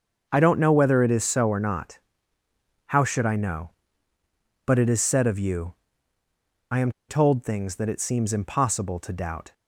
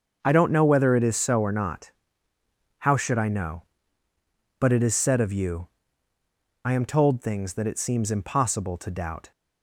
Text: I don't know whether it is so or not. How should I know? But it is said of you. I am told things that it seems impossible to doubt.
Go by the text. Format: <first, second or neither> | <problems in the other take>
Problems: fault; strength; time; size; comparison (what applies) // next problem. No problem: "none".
second | starts louder than the rest; until 1.3 s; 6.5 dB; also in the second // pauses between "am" and "told"; slight; at 6.9 s; 0.17 s long